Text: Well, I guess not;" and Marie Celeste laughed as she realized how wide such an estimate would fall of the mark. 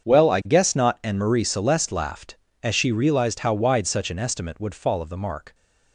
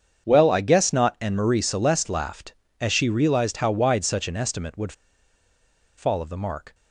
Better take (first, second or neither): first